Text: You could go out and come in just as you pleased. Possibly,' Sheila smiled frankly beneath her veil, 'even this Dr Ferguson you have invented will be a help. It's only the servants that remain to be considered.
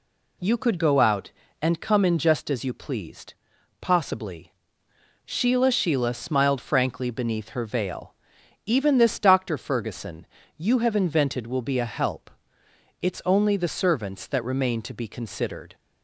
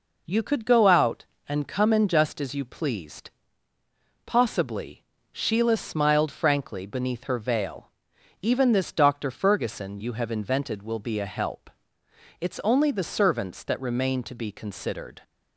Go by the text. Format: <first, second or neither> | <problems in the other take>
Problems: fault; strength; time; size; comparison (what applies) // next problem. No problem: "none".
second | says "Sheila" twice; at 5.7 s // pauses between "Ferguson" and "you"; slight; at 10.2 s; 0.32 s long